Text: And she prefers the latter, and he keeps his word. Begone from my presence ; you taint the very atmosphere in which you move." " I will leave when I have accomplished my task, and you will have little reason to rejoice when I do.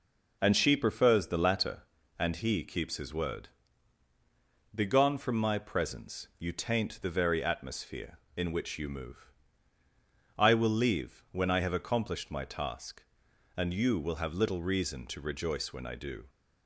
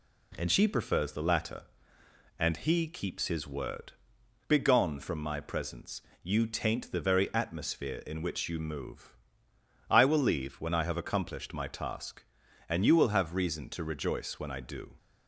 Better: first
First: none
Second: skips "little"; at 13.3 s

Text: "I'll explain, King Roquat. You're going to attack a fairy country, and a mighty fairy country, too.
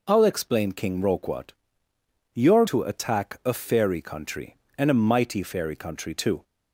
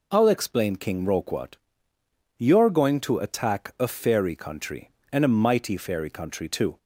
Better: second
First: skips "going"; at 2.6 s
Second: none

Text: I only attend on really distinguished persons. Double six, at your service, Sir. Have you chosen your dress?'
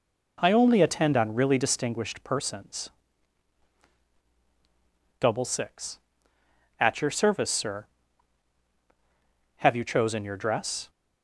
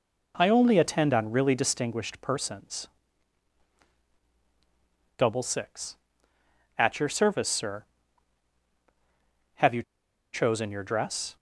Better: first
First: none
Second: pauses between "you" and "chosen"; noticeable; at 9.8 s; 0.51 s long

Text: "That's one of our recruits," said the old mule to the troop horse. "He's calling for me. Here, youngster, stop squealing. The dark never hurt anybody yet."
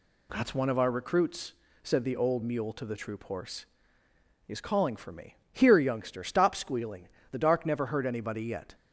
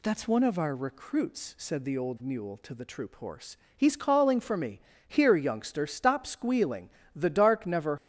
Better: first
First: none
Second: stops before "hurt anybody yet"; at 7.9 s

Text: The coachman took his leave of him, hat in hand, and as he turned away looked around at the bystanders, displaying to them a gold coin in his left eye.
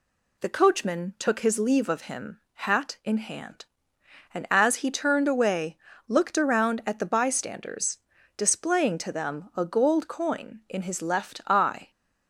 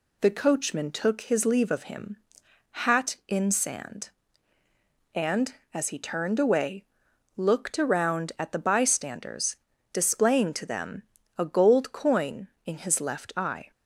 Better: first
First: pauses between "away" and "looked"; slight; at 5.7 s; 0.30 s long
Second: says "sand" for "hand"; at 3.5 s // pauses between "away" and "looked"; noticeable; at 6.8 s; 0.52 s long // pauses between "them" and "a"; slight; at 11.0 s; 0.34 s long

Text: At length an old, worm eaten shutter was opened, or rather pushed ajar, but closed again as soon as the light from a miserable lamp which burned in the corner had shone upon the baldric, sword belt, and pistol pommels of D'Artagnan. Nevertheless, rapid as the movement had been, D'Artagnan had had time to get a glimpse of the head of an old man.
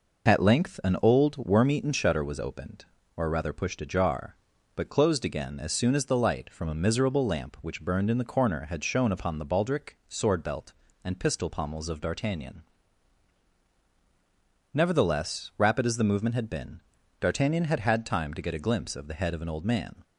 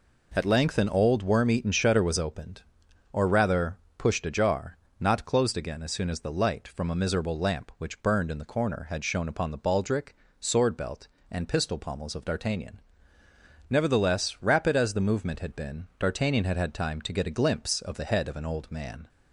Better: first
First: none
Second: pauses between "rather" and "pushed"; slight; at 3.7 s; 0.22 s long // says "not" for "but"; at 4.9 s

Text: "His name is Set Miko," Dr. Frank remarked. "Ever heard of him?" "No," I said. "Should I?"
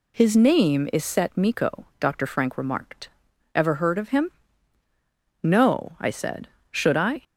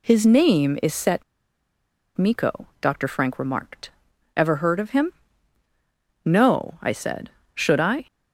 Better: first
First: none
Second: pauses between "Set" and "Miko"; noticeable; at 1.2 s; 0.93 s long

